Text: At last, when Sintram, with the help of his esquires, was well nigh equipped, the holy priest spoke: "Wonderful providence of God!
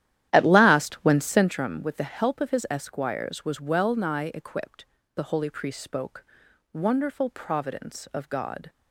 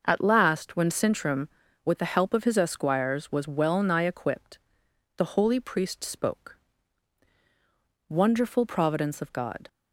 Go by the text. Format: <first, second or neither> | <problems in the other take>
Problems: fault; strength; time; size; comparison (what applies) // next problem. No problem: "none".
second | starts louder than the rest; strong; until 1.5 s; 12 dB